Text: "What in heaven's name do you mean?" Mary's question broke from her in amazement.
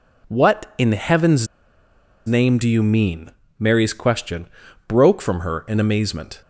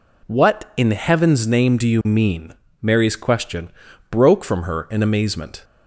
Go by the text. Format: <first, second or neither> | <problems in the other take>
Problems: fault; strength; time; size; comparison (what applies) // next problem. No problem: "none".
second | pauses between "heaven's" and "name"; noticeable; at 1.4 s; 0.80 s long // pauses between "question" and "broke"; at 4.4 s; 0.40 s long; also in the second